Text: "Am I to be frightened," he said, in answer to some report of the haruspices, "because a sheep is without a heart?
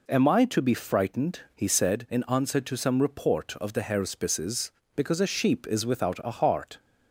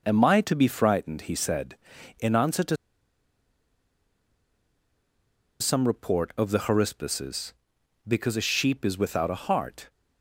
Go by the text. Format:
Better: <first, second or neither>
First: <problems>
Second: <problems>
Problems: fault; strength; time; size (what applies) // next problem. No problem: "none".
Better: first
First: none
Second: pauses between "to" and "some"; strong; at 2.7 s; 2.8 s long